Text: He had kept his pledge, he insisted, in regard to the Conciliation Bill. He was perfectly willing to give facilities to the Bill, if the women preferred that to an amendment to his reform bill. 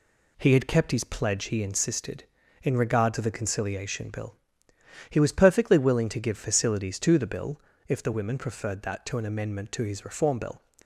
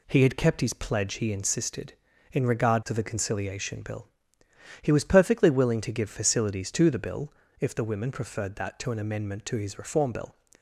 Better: neither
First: none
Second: none

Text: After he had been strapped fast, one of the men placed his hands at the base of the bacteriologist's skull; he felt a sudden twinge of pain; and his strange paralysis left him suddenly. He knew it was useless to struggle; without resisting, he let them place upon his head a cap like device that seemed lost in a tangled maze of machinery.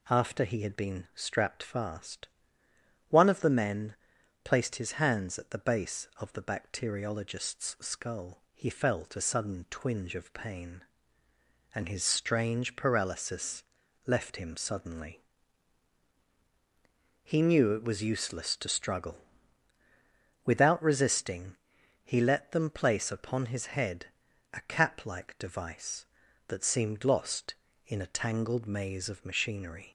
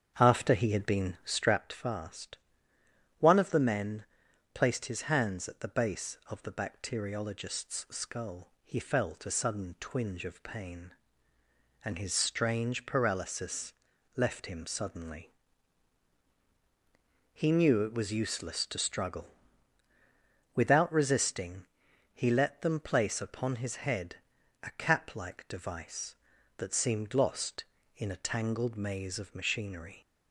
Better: first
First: pauses between "men" and "placed"; noticeable; at 3.9 s; 0.48 s long // pauses between "paralysis" and "left"; at 13.6 s; 0.42 s long // pauses between "head" and "a"; noticeable; at 24.0 s; 0.46 s long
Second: starts louder than the rest; strong; until 1.7 s; 7.5 dB // pauses between "men" and "placed"; noticeable; at 4.0 s; 0.48 s long // pauses between "paralysis" and "left"; at 13.7 s; 0.42 s long // pauses between "head" and "a"; noticeable; at 24.1 s; 0.46 s long

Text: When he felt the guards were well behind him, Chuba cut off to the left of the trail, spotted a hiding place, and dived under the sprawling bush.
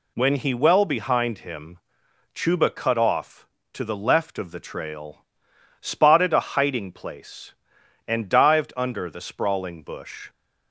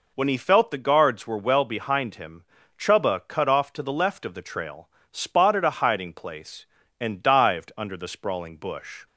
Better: second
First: skips "felt the guards were"; at 0.5 s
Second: none

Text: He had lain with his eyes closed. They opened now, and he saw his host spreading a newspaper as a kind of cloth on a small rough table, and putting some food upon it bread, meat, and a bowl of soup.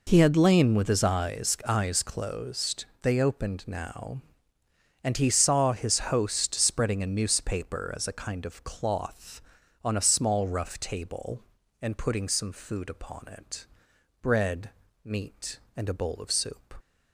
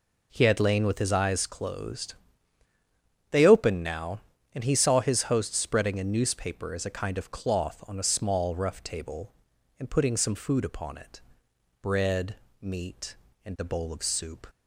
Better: second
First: says "eyes" twice; at 1.6 s // pauses between "it" and "bread"; noticeable; at 13.6 s; 0.56 s long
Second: pauses between "it" and "bread"; noticeable; at 11.2 s; 0.60 s long

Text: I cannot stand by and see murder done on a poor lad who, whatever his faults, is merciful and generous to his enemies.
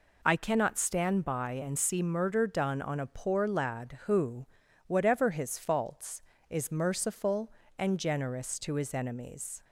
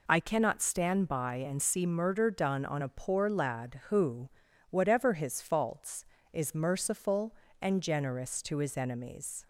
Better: neither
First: none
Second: none

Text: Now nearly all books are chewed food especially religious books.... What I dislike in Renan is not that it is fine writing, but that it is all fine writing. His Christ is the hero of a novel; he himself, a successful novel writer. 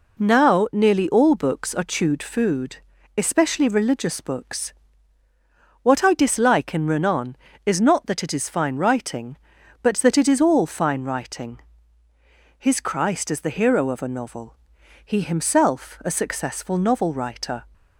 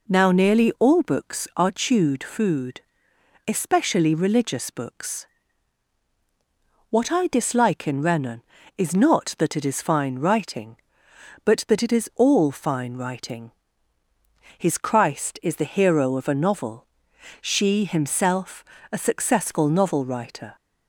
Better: first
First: pauses between "food" and "especially"; at 2.7 s; 0.38 s long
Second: pauses between "food" and "especially"; noticeable; at 2.8 s; 0.66 s long // says "she" for "he"; at 17.3 s

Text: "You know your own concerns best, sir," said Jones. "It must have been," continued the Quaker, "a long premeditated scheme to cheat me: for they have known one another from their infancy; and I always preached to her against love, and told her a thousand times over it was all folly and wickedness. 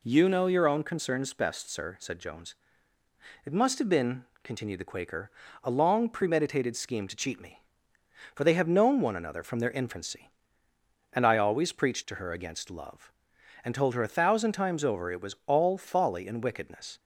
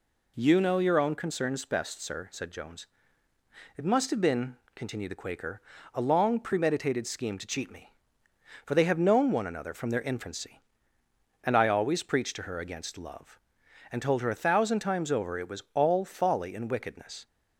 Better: neither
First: none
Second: none

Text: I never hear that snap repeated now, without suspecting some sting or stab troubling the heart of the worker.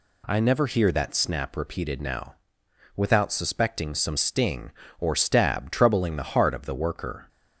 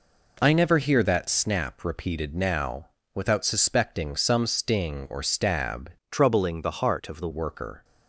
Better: first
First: none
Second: changes voice from "troubling" to "the"; from 6.1 to 7.2 s; 1.1 s long

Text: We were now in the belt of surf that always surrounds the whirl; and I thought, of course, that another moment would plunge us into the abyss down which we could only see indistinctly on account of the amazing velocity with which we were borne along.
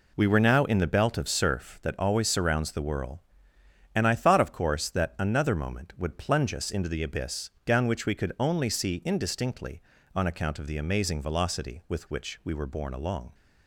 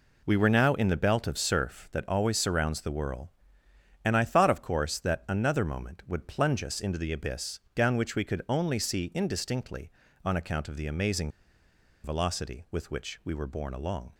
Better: first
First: pauses between "abyss" and "down"; slight; at 7.4 s; 0.16 s long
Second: pauses between "abyss" and "down"; slight; at 7.5 s; 0.16 s long // pauses between "amazing" and "velocity"; noticeable; at 11.2 s; 0.75 s long

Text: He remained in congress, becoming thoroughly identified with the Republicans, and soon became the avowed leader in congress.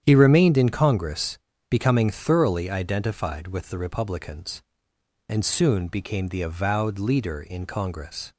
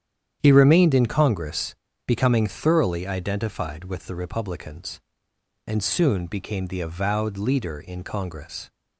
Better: neither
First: starts louder than the rest; strong; until 1.0 s; 9.5 dB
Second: starts louder than the rest; strong; until 1.4 s; 9.5 dB

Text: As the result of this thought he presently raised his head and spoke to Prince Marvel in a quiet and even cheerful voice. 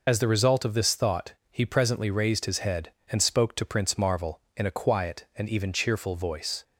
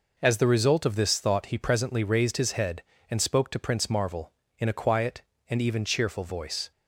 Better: second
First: loses the start of "As"; at 0.0 s; 60 ms // pauses between "thought" and "he"; slight; at 1.3 s; 0.18 s long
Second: none

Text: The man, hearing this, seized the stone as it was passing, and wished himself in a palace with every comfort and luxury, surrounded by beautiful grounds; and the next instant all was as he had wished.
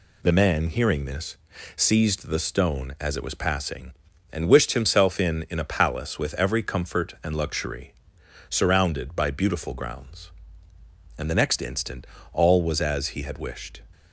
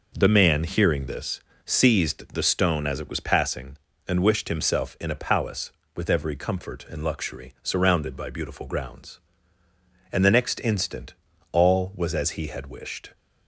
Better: second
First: says "in" twice; at 5.4 s // pauses between "instant" and "all"; slight; at 12.0 s; 0.28 s long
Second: pauses between "instant" and "all"; slight; at 11.1 s; 0.36 s long

